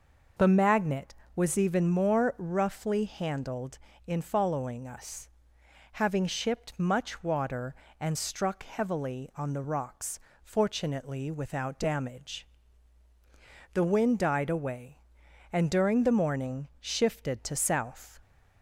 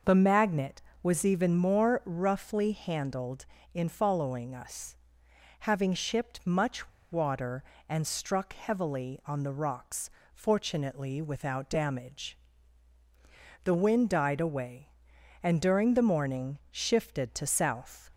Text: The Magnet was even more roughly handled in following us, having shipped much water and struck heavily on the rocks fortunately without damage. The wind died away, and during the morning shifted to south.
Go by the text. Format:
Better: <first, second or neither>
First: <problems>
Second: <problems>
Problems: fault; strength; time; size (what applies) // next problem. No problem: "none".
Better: first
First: pauses between "rocks" and "fortunately"; slight; at 10.1 s; 0.24 s long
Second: pauses between "much" and "water"; slight; at 6.8 s; 0.22 s long // pauses between "rocks" and "fortunately"; slight; at 10.1 s; 0.24 s long